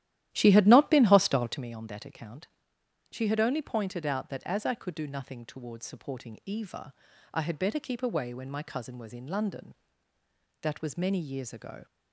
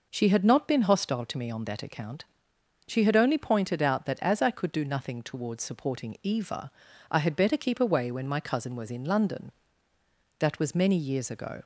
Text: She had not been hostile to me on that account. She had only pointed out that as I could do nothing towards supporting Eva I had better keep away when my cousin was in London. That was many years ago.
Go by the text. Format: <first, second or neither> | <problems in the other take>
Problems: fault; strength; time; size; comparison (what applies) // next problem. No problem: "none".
second | starts louder than the rest; strong; until 1.7 s; 13 dB // pauses between "Eva" and "I"; at 6.9 s; 0.40 s long; also in the second